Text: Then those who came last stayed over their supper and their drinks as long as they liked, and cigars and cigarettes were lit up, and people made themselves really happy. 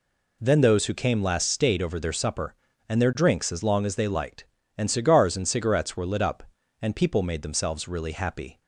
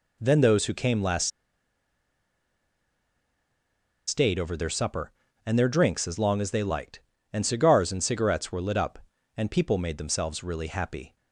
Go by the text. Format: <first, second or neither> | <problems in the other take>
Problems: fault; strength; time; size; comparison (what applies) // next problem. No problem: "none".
first | pauses between "last" and "stayed"; strong; at 1.3 s; 2.7 s long